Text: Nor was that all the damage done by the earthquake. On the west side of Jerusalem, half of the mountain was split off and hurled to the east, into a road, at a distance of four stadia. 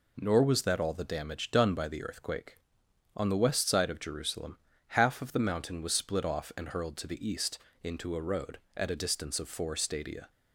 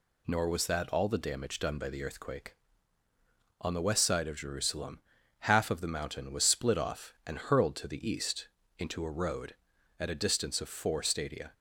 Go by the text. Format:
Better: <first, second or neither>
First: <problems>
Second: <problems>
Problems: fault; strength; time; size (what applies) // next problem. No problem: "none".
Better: neither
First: none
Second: none